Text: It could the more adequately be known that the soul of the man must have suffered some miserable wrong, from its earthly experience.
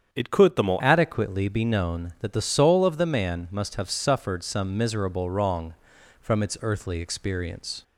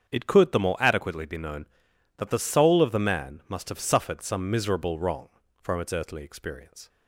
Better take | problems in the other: second | starts louder than the rest; strong; until 1.1 s; 8 dB; strong in the second // changes voice at "adequately"; from 0.7 s on; 7.1 s long

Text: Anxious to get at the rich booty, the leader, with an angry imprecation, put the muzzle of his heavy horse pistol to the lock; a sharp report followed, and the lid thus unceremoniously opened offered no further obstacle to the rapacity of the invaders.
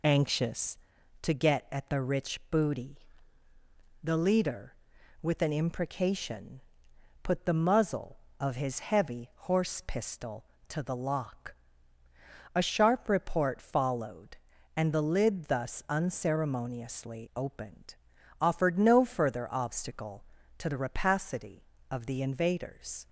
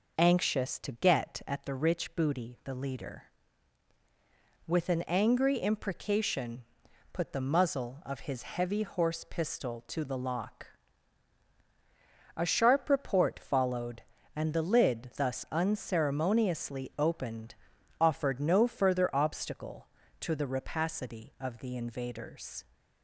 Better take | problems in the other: second | skips "angry"; at 5.5 s // pauses between "opened" and "offered"; at 17.9 s; 0.44 s long; also in the second

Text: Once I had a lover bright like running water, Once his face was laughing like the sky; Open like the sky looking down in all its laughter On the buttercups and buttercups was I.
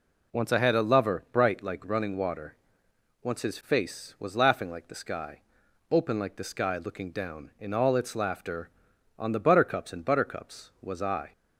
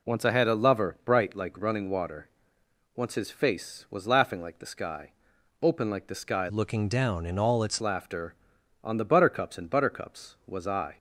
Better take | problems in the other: first | changes voice from "looking" to "its"; from 6.4 to 7.8 s; 1.4 s long

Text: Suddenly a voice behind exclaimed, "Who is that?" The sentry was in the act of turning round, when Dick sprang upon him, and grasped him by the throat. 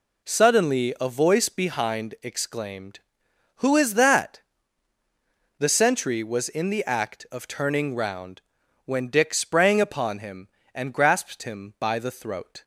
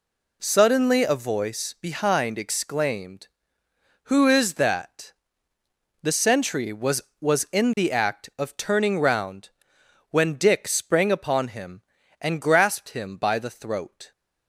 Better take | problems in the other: first | says "was" twice; at 7.1 s

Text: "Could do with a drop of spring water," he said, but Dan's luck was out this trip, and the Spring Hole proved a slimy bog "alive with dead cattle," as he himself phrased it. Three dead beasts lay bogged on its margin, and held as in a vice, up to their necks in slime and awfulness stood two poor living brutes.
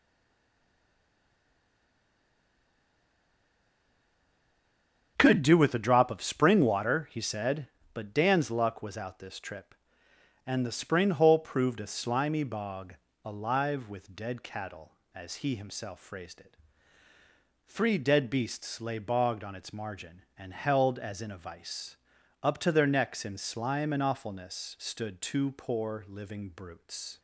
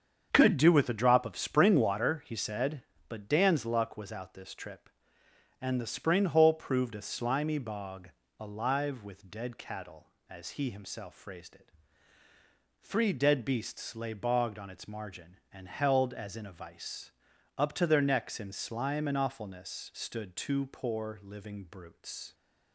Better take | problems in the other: second | stays silent before the first word; strong; until 5.1 s; 5.1 s long // starts louder than the rest; strong; until 6.1 s; 7 dB; strong in the second // pauses between "bog" and "alive"; slight; at 12.9 s; 0.28 s long; slight in the second

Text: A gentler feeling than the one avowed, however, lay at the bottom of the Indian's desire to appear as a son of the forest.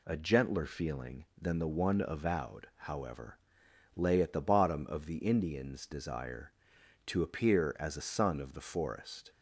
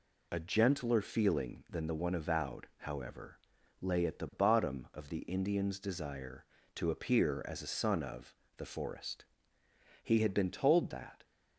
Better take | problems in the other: first | pauses between "of" and "the"; slight; at 8.3 s; 0.22 s long // goes on to say "He had been told that"; noticeable; from 10.0 s on; 1.2 s long

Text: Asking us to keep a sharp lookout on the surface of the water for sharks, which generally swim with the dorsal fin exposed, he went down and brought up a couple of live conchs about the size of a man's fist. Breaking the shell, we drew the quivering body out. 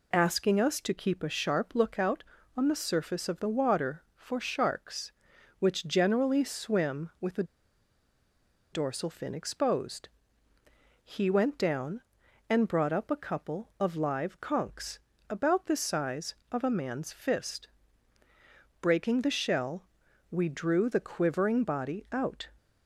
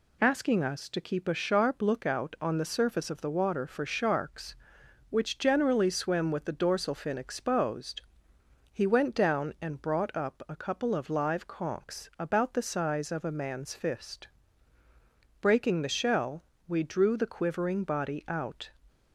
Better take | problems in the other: second | pauses between "the" and "dorsal"; strong; at 7.4 s; 1.2 s long // pauses between "conchs" and "about"; slight; at 14.9 s; 0.32 s long

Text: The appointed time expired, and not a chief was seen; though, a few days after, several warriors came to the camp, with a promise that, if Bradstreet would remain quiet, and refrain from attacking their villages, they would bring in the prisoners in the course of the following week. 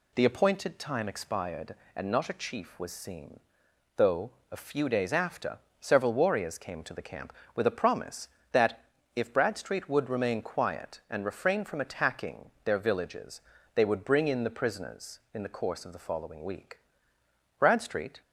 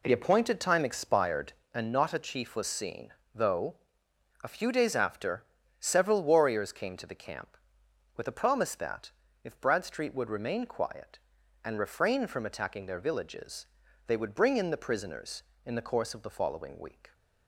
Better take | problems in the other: second | goes on to say "Bradstreet"; noticeable; from 17.5 s on; 0.62 s long

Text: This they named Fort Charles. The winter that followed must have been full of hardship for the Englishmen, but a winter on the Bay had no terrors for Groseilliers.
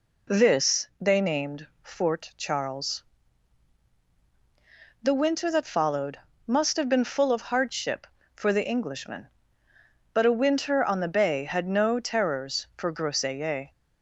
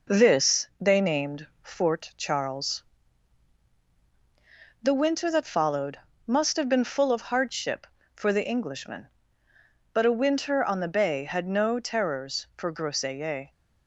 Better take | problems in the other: first | gets quieter; slight; throughout; 2.5 dB // pauses between "followed" and "must"; slight; at 5.9 s; 0.28 s long; slight in the first

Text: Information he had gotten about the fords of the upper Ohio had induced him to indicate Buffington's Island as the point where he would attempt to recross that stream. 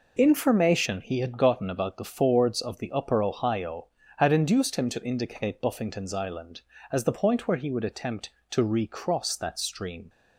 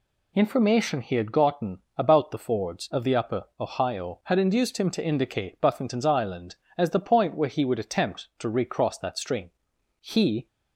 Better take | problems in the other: first | pauses between "gotten" and "about"; slight; at 1.7 s; 0.16 s long // pauses between "upper" and "Ohio"; slight; at 3.4 s; 0.16 s long // goes on to say "He"; slight; from 10.0 s on; 0.46 s long

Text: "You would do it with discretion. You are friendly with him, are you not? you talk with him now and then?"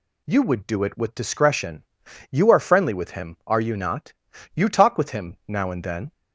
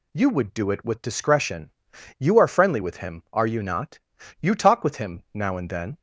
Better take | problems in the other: neither | none

